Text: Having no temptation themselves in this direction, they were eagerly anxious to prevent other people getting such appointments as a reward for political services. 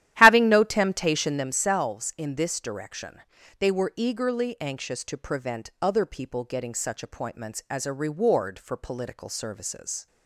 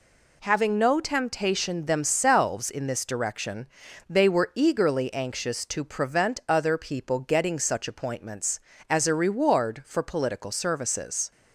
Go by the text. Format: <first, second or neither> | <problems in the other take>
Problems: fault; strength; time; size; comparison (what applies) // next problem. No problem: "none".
second | starts louder than the rest; strong; until 1.5 s; 12.5 dB